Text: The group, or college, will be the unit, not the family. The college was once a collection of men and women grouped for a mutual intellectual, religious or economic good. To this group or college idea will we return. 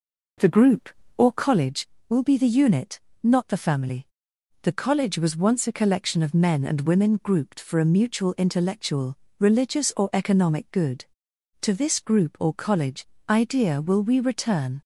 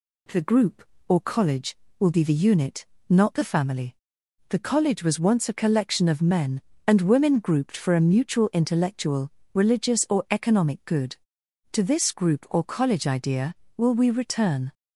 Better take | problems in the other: second | starts louder than the rest; noticeable; until 1.6 s; 4.5 dB // pauses between "college" and "idea"; slight; at 13.0 s; 0.24 s long

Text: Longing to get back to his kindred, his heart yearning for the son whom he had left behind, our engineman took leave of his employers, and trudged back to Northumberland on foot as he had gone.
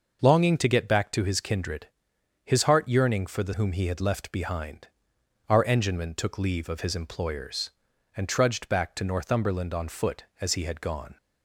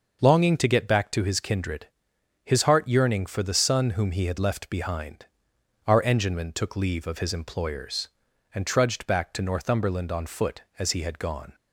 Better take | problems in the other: second | skips "son"; at 3.5 s

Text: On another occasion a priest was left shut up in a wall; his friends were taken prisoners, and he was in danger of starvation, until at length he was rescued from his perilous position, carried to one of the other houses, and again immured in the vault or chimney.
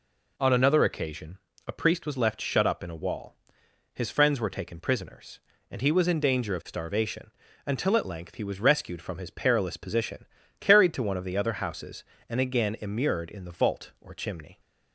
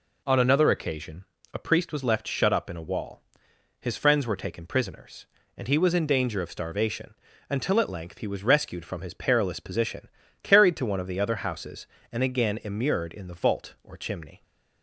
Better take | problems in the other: neither | pauses between "occasion" and "a"; slight; the same in both

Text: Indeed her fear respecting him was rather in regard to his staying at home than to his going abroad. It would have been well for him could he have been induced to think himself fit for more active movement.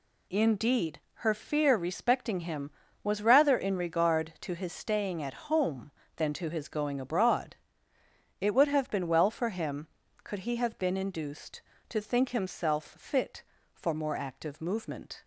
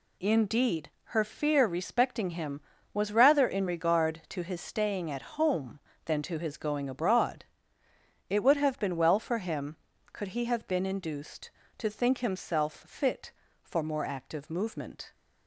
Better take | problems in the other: neither | pauses between "Indeed" and "her"; slight; the same in both

